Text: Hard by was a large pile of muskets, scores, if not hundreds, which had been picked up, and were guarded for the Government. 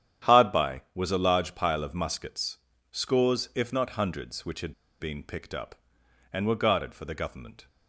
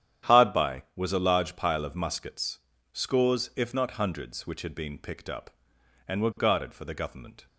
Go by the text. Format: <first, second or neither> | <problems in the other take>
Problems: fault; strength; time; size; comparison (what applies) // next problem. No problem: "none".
second | starts louder than the rest; strong; until 1.3 s; 10 dB; strong in the second // pauses between "had" and "been"; slight; at 4.7 s; 0.27 s long